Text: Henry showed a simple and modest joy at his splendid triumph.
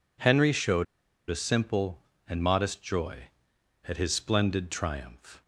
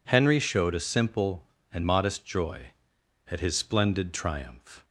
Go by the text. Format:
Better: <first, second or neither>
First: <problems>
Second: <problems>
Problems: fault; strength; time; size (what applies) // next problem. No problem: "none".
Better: second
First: pauses between "showed" and "a"; at 0.8 s; 0.42 s long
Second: none